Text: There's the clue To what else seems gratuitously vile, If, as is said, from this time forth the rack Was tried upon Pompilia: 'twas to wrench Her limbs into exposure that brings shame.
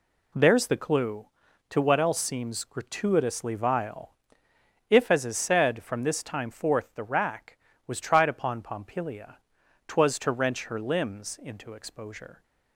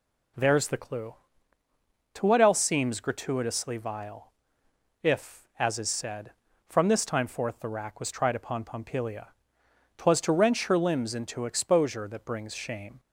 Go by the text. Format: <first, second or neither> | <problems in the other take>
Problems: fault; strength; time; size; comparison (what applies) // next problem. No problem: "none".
second | stops before "that brings shame"; at 12.4 s